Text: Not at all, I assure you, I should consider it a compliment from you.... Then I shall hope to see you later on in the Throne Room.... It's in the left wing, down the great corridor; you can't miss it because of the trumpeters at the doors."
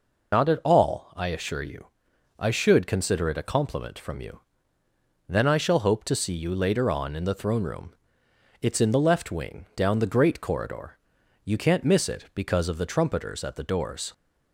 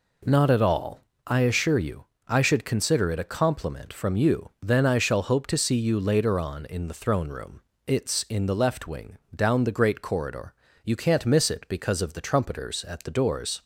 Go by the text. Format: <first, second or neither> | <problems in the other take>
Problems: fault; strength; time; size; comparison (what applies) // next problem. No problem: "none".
second | loses the start of "Not"; at 0.3 s; 95 ms